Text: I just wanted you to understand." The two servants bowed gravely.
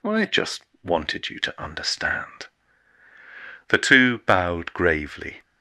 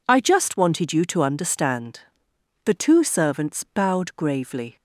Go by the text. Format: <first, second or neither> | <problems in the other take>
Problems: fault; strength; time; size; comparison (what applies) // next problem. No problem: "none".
second | pauses between "just" and "wanted"; slight; at 0.6 s; 0.20 s long // skips "servants"; at 4.1 s